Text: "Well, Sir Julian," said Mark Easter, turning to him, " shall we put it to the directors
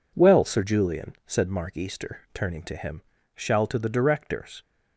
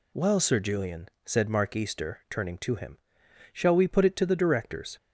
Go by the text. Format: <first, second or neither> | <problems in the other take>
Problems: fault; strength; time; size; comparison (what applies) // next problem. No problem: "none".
second | skips "we put it"; at 3.6 s